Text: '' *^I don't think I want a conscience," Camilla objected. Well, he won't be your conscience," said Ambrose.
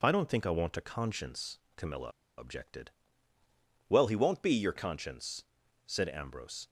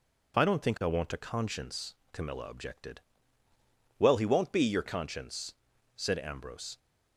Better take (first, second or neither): second